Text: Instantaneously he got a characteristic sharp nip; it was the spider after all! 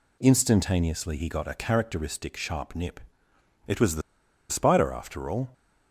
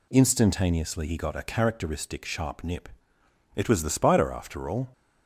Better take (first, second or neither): second